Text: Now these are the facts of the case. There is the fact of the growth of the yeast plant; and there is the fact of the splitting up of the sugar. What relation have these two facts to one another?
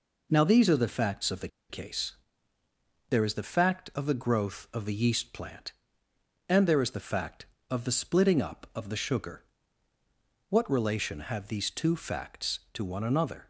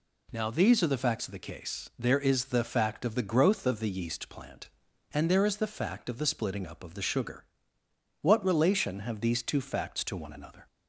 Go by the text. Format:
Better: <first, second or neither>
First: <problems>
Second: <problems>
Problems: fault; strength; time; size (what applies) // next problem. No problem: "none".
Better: second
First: pauses between "the" and "case"; slight; at 1.4 s; 0.21 s long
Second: none